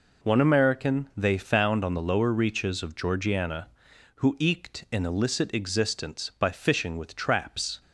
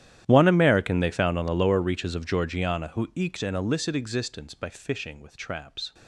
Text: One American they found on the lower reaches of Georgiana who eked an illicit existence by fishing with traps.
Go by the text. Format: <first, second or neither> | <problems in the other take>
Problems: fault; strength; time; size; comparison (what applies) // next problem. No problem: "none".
first | gets quieter; strong; throughout; 22 dB